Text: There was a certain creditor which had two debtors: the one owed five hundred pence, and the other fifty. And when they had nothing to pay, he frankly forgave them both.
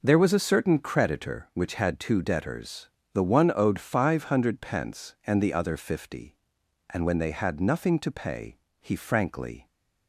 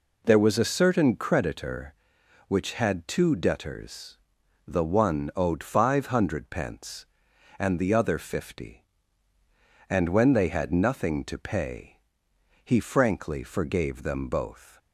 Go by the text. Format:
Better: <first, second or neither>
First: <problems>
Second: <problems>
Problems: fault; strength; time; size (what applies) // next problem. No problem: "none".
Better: second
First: stops before "forgave them both"; at 9.6 s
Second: none